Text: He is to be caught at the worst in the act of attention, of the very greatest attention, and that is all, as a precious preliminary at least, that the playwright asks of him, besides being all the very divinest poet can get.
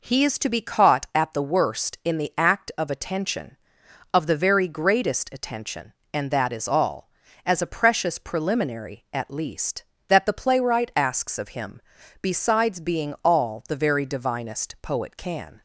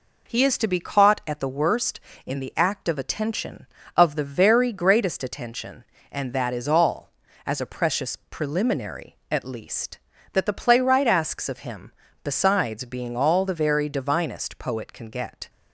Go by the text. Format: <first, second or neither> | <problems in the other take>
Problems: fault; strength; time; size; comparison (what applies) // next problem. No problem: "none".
second | stops before "get"; at 15.5 s